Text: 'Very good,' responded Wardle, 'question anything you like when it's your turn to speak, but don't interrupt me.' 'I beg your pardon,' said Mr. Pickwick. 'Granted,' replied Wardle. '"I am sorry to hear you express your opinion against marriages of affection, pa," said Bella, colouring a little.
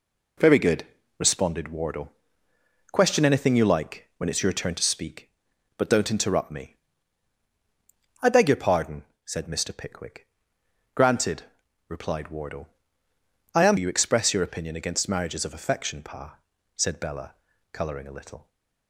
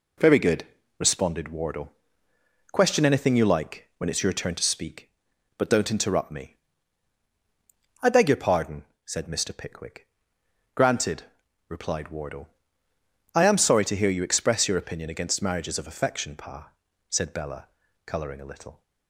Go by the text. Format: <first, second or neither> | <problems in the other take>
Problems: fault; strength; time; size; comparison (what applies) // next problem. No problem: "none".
second | skips "sorry to hear"; at 13.7 s